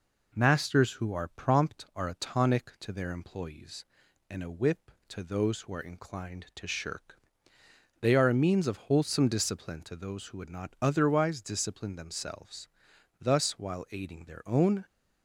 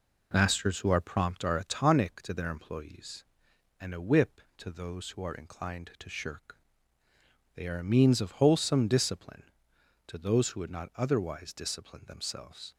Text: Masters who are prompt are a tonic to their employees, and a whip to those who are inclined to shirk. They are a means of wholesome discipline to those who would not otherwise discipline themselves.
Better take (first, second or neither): second